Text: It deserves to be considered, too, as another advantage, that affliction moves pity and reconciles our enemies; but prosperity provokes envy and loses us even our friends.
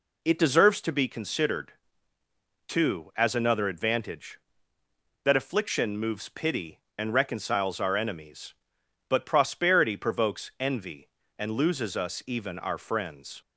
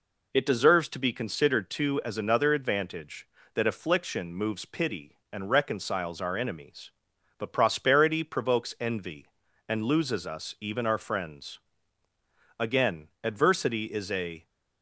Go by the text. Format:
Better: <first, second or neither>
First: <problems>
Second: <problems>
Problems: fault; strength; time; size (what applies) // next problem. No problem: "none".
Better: first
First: none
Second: goes on to say "Again adversity is a"; strong; from 12.5 s on; 1.8 s long